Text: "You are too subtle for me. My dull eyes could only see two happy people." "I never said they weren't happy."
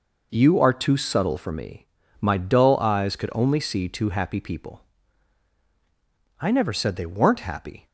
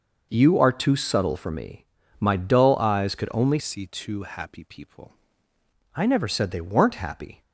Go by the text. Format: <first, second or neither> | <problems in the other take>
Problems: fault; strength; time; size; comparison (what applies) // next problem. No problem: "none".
first | changes voice from "see" to "people"; from 3.5 to 5.1 s; 1.6 s long